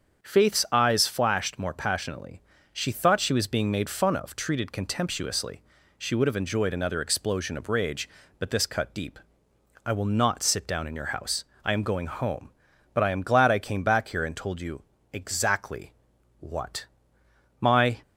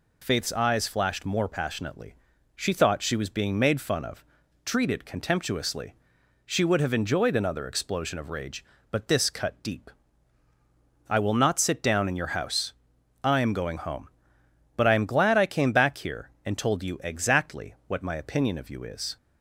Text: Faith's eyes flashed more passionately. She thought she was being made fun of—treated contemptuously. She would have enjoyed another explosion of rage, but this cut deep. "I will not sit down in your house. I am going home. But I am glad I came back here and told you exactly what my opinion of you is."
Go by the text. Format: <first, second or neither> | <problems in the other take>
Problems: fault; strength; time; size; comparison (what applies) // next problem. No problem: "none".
second | starts louder than the rest; strong; until 1.2 s; 7.5 dB // pauses between "you" and "exactly"; slight; at 14.8 s; 0.30 s long // pauses between "exactly" and "what"; noticeable; at 15.9 s; 0.46 s long // pauses between "what" and "my"; noticeable; at 16.8 s; 0.74 s long // stops before "opinion of you is"; at 18.0 s